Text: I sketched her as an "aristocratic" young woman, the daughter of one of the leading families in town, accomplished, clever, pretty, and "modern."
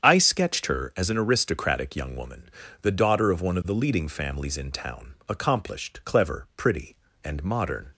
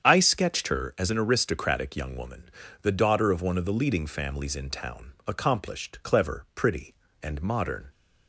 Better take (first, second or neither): neither